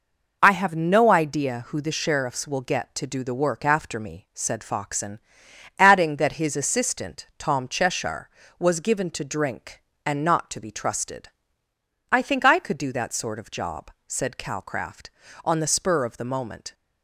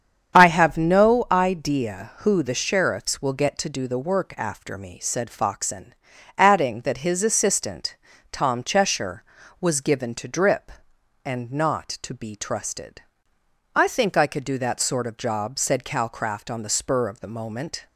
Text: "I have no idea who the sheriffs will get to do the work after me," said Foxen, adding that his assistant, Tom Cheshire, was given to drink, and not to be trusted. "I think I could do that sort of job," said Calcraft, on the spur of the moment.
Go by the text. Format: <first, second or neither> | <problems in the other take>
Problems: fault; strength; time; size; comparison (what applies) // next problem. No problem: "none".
first | starts louder than the rest; strong; until 1.4 s; 8 dB // says "drip" for "drink"; at 10.2 s